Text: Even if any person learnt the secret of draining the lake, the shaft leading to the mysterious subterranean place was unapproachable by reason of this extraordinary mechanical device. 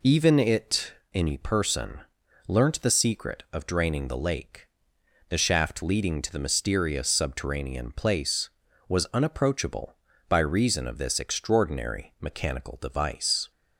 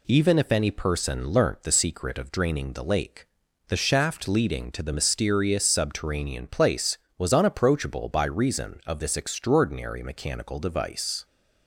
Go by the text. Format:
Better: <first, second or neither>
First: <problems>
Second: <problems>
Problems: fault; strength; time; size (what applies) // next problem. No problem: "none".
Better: second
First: says "it" for "if"; at 0.3 s // pauses between "person" and "learnt"; noticeable; at 1.9 s; 0.48 s long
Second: none